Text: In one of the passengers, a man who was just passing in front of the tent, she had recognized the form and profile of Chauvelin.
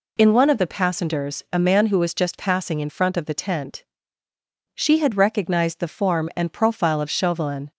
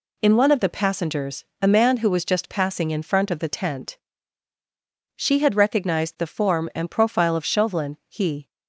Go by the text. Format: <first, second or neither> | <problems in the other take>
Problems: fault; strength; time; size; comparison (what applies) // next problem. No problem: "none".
first | goes on to say "He"; slight; from 8.0 s on; 0.40 s long